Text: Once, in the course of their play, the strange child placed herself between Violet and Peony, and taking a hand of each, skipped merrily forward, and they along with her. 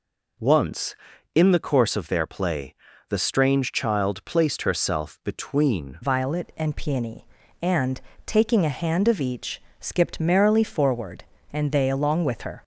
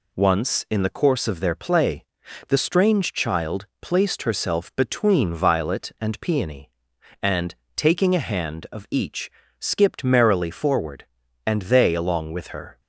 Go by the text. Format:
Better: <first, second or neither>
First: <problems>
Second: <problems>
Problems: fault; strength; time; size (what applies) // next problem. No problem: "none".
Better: second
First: changes voice at "Violet"; from 6.0 s on; 6.6 s long // pauses between "and" and "taking"; slight; at 7.9 s; 0.28 s long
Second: pauses between "and" and "taking"; slight; at 7.5 s; 0.22 s long